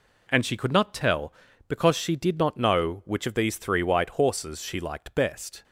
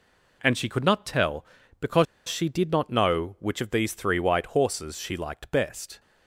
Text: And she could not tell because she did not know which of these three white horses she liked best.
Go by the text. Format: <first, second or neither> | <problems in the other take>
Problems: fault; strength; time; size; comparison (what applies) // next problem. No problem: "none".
first | pauses between "because" and "she"; slight; at 2.0 s; 0.22 s long